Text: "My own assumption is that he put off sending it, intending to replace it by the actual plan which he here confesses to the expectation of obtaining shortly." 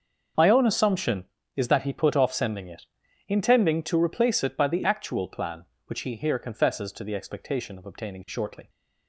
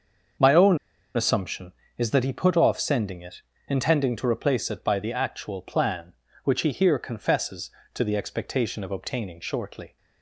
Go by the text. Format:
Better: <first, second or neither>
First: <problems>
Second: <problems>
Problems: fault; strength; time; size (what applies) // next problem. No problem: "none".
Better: first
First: starts louder than the rest; until 1.6 s; 6.5 dB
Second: starts louder than the rest; until 2.0 s; 6.5 dB // pauses between "own" and "assumption"; at 0.7 s; 0.38 s long